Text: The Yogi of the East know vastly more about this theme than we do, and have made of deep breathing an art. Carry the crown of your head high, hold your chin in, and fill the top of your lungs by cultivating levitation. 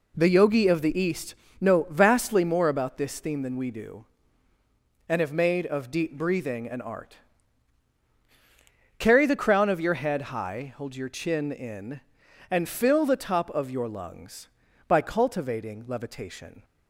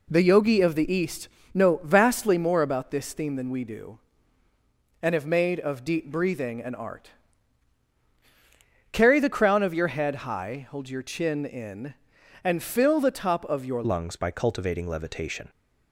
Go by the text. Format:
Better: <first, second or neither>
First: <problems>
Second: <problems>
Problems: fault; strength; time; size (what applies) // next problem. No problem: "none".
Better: first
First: pauses between "East" and "know"; slight; at 1.3 s; 0.24 s long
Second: pauses between "East" and "know"; slight; at 1.2 s; 0.24 s long // changes voice at "lungs"; from 13.8 s on; 1.6 s long